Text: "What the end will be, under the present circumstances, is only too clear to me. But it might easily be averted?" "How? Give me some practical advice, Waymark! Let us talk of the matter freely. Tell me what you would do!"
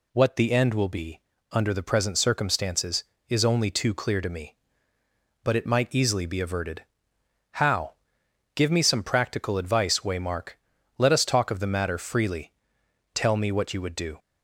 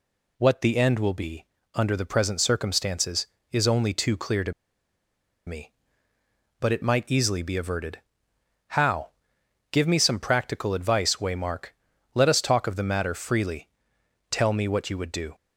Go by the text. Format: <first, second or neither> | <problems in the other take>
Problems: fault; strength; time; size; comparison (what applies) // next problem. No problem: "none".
first | pauses between "to" and "me"; noticeable; at 4.5 s; 0.95 s long